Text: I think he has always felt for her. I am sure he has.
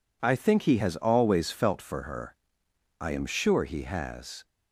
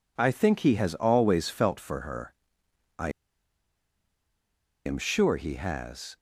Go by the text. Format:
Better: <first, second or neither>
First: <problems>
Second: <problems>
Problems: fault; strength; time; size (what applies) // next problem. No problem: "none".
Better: first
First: none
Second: pauses between "I" and "am"; strong; at 3.0 s; 1.7 s long